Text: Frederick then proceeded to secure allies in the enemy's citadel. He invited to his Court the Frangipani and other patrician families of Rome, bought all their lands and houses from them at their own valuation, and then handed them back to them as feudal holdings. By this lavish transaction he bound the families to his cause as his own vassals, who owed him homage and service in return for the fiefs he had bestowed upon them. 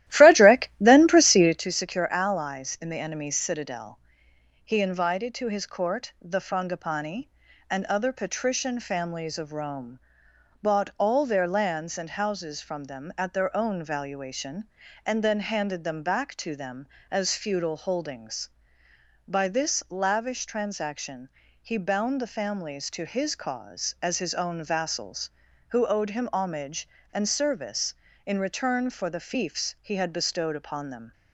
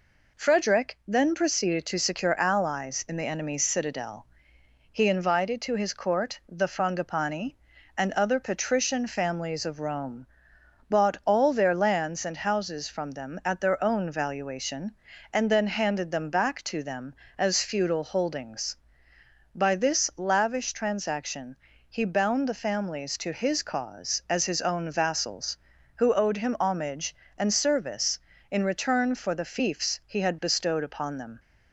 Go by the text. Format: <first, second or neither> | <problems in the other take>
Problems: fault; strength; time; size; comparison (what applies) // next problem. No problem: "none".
second | starts louder than the rest; strong; until 1.7 s; 14 dB // pauses between "transaction" and "he"; slight; at 21.2 s; 0.32 s long; slight in the second